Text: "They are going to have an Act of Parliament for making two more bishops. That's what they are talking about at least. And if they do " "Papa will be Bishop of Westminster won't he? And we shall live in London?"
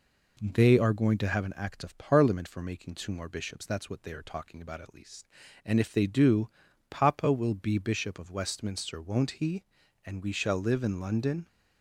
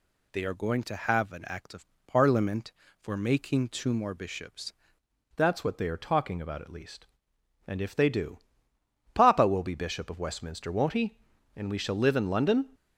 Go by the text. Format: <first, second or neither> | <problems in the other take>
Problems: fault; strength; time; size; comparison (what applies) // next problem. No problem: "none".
first | pauses between "of" and "Parliament"; slight; at 1.8 s; 0.18 s long // changes voice at "That's"; from 5.3 s on; 7.3 s long